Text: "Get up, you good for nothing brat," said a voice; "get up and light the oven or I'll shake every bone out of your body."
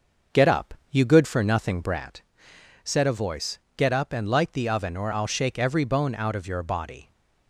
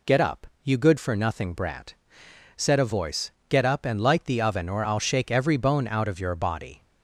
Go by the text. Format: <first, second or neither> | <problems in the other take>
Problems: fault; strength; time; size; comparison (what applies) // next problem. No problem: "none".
second | starts louder than the rest; noticeable; until 2.2 s; 6 dB